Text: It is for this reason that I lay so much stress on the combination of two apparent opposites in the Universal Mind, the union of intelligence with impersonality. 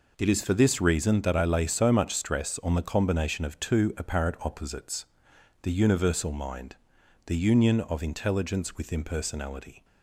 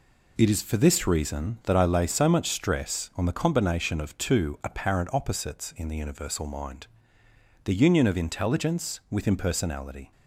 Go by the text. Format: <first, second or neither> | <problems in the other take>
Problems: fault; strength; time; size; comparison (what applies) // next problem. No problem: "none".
second | skips "in"; at 5.3 s